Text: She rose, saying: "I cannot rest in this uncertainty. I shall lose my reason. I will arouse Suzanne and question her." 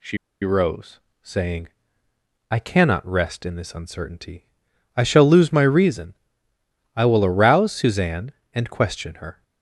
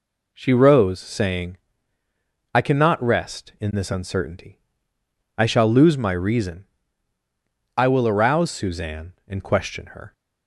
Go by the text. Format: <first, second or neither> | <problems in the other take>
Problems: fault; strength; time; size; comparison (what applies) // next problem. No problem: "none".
second | pauses between "She" and "rose"; slight; at 0.1 s; 0.25 s long